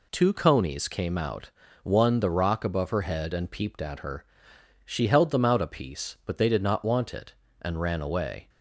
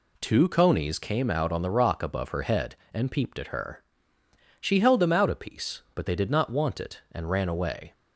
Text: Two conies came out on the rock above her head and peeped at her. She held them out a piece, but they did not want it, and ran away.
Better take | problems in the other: second | says "one" for "on"; at 1.8 s

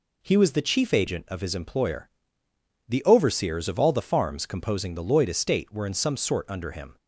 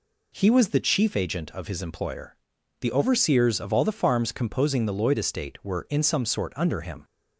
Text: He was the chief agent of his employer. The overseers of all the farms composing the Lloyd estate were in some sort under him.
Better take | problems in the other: neither | none

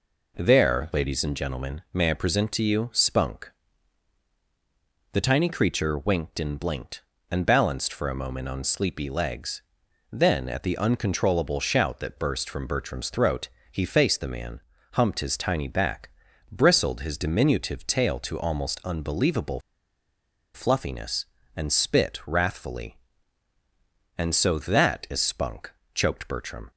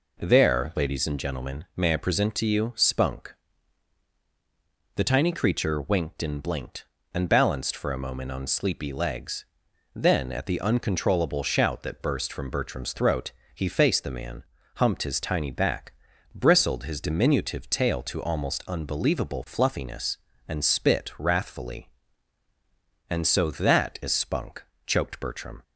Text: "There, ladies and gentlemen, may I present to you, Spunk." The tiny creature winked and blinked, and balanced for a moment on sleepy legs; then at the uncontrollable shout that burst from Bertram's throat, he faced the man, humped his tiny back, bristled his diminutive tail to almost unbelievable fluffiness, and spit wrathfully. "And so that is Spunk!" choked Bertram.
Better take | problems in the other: second | pauses between "unbelievable" and "fluffiness"; noticeable; at 19.6 s; 0.93 s long

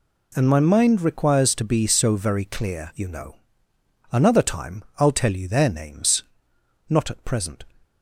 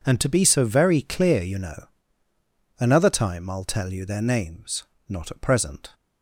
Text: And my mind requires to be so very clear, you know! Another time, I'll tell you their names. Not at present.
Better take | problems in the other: first | skips "my mind requires"; at 0.2 s

